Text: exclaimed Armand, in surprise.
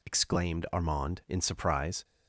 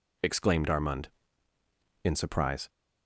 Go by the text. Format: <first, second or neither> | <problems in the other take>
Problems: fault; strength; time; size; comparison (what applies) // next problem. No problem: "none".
neither | none